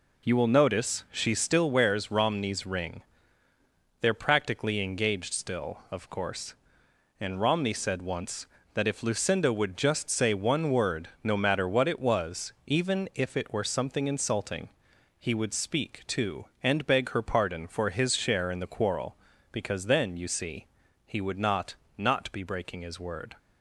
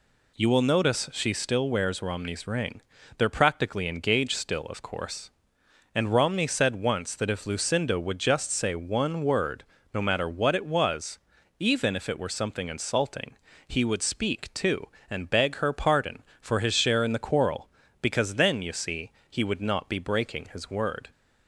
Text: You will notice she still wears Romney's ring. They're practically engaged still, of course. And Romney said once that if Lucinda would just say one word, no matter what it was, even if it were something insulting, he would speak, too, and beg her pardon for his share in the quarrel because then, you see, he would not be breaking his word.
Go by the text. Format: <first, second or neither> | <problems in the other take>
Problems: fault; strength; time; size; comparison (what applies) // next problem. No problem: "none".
second | says "not" twice; at 21.9 s